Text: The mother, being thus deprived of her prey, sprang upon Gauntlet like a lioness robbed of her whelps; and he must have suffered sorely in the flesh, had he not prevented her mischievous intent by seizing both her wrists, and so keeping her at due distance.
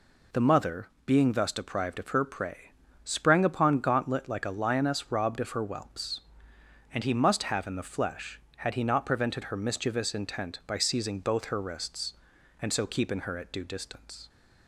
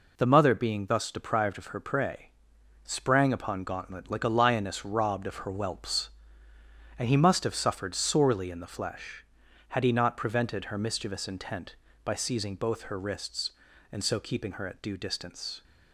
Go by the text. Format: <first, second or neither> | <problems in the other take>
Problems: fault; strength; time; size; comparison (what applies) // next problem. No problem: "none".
second | skips "suffered sorely"; at 7.6 s